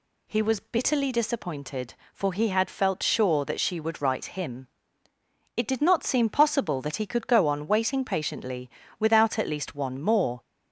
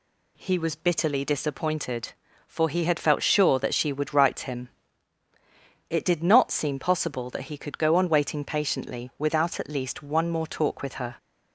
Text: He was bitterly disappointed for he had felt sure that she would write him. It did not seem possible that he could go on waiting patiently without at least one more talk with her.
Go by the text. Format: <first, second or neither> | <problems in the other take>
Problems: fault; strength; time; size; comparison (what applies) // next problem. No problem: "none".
second | pauses between "patiently" and "without"; slight; at 8.6 s; 0.30 s long // stops before "talk with her"; at 10.4 s